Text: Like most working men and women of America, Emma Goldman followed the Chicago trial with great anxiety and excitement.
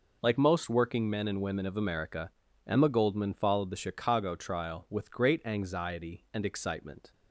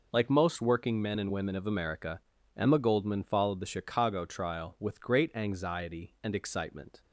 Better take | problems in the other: neither | none

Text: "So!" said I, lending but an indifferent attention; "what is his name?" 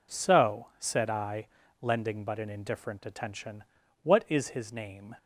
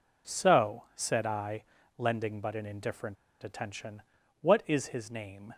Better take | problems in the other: first | pauses between "indifferent" and "attention"; slight; at 3.1 s; 0.27 s long

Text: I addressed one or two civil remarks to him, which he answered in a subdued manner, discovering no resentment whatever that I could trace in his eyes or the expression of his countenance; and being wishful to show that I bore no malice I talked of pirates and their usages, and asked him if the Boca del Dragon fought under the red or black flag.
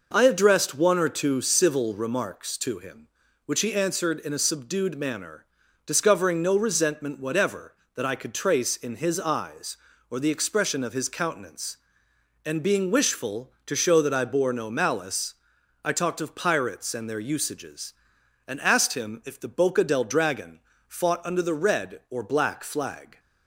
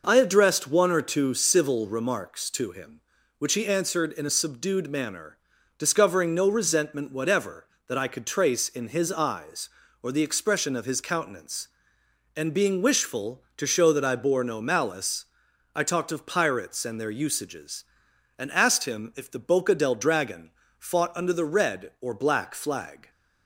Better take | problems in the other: neither | pauses between "malice" and "I"; noticeable; the same in both // pauses between "Dragon" and "fought"; slight; the same in both

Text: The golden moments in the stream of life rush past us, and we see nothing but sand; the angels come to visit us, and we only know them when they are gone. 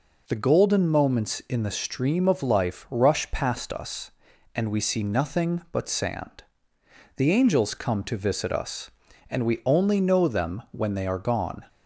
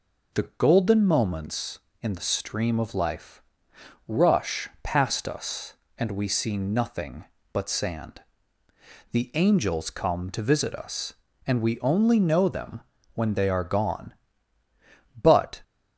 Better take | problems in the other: first | pauses between "life" and "rush"; noticeable; at 3.3 s; 0.68 s long // pauses between "them" and "when"; slight; at 12.7 s; 0.34 s long // goes on to say "But"; slight; from 15.2 s on; 0.40 s long

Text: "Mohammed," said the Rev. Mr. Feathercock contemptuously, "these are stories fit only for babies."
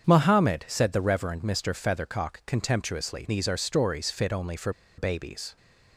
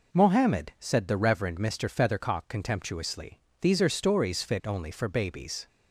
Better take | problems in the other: second | starts louder than the rest; strong; until 1.1 s; 7.5 dB // pauses between "for" and "babies"; slight; at 4.7 s; 0.26 s long

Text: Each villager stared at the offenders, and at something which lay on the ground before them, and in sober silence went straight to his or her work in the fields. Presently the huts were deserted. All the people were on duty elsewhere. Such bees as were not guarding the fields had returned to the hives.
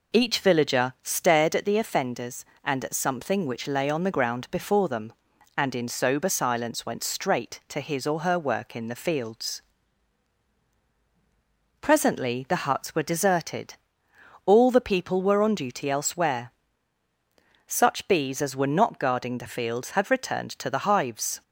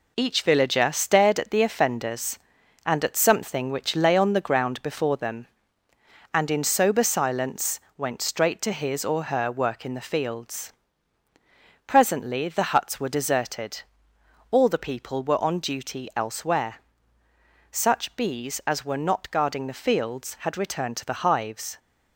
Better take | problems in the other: first | gets quieter; noticeable; throughout; 5.5 dB // pauses between "silence" and "went"; slight; at 7.8 s; 0.16 s long

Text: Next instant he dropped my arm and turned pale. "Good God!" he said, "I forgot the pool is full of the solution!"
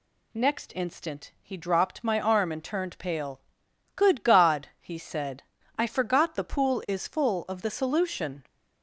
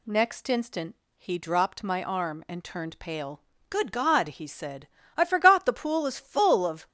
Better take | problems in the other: first | pauses between "instant" and "he"; slight; at 0.9 s; 0.20 s long // stops before "the solution"; at 6.8 s

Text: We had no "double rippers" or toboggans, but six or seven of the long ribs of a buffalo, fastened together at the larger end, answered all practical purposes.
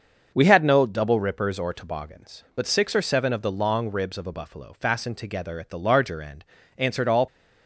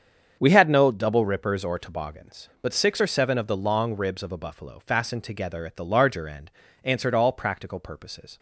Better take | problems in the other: second | starts louder than the rest; until 1.3 s; 6.5 dB; strong in the second // stops before "practical purposes"; at 7.2 s

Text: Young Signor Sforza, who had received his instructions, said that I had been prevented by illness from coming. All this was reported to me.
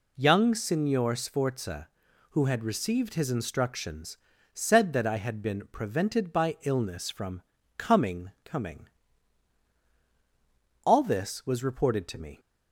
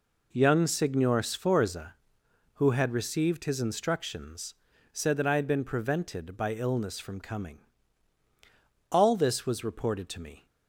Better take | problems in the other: second | pauses between "from" and "coming"; slight; at 7.4 s; 0.34 s long // says "coming" twice; at 8.4 s

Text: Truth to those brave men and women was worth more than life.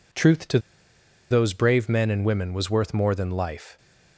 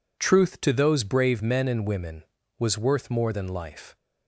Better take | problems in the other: second | pauses between "to" and "those"; noticeable; at 0.5 s; 0.71 s long

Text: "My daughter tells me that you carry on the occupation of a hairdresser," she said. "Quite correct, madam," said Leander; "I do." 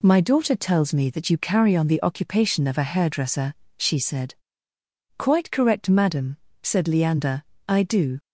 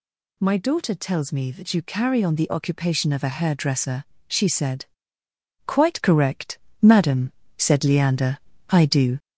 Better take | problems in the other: first | gets louder; noticeable; throughout; 4.5 dB

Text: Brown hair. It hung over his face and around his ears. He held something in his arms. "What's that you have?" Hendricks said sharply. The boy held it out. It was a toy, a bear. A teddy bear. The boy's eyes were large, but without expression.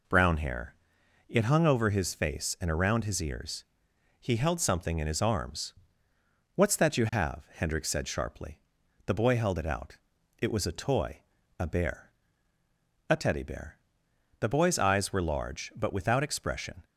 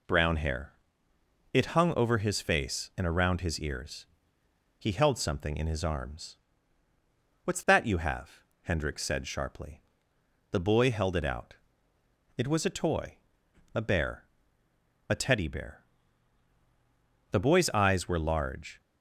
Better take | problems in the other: first | stops before "but without expression"; at 18.8 s

